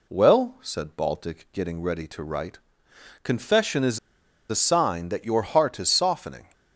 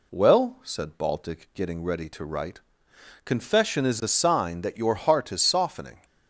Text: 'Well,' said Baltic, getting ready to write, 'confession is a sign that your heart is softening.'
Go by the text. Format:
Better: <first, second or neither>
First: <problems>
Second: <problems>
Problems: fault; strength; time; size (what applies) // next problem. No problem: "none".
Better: second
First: pauses between "is" and "a"; noticeable; at 3.9 s; 0.51 s long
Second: none